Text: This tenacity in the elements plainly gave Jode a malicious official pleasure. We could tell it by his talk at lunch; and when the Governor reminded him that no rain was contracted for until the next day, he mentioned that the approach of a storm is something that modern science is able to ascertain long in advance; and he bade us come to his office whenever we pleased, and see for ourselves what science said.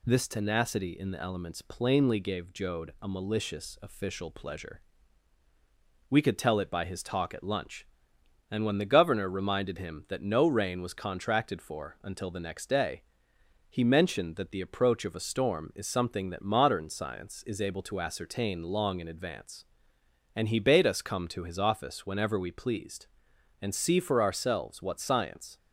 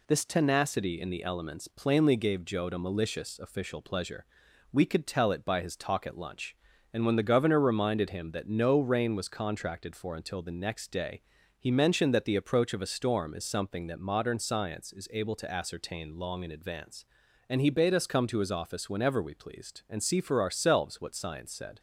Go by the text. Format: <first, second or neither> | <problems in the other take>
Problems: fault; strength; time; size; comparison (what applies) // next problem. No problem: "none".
second | stops before "said"; at 25.5 s